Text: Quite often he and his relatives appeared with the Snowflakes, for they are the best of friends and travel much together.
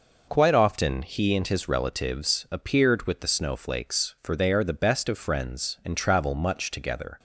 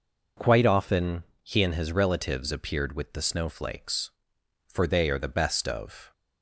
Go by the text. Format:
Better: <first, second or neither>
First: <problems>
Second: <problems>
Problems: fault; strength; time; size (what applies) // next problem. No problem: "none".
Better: first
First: none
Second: pauses between "often" and "he"; slight; at 1.2 s; 0.18 s long // stops before "friends and travel much together"; at 6.1 s